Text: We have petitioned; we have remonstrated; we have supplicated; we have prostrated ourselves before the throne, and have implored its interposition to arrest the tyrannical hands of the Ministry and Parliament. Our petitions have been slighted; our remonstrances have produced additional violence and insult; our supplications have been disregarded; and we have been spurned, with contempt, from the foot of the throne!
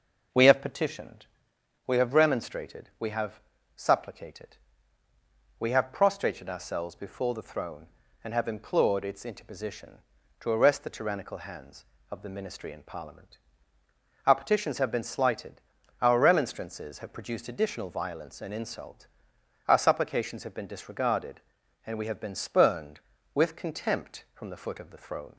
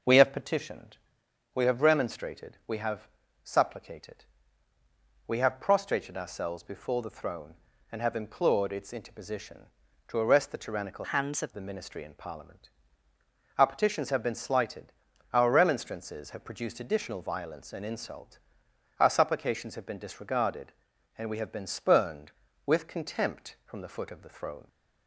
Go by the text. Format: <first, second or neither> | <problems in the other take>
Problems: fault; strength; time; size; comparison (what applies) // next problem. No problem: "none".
first | pauses between "have" and "supplicated"; slight; at 3.0 s; 0.36 s long; slight in the first // changes voice from "hands" to "of"; from 11.1 to 11.5 s; 0.4 s long